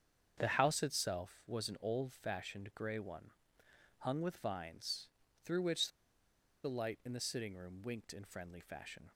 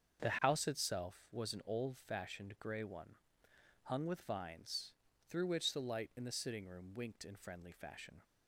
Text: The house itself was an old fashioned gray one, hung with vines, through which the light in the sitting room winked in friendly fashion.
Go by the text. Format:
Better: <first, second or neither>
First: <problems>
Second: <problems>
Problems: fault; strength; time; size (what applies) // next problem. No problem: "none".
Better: second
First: starts louder than the rest; strong; until 1.3 s; 7.5 dB // pauses between "which" and "the"; noticeable; at 5.8 s; 0.75 s long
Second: starts louder than the rest; strong; until 1.2 s; 7.5 dB